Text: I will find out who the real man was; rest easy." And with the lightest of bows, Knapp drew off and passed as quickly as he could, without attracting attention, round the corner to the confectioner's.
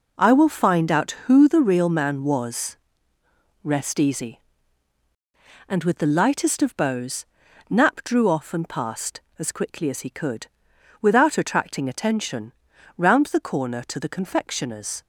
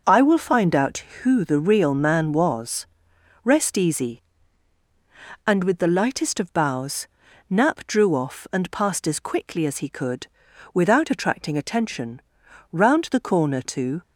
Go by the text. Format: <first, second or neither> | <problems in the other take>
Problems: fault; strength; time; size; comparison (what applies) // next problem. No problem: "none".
first | stops before "the confectioner's"; at 14.0 s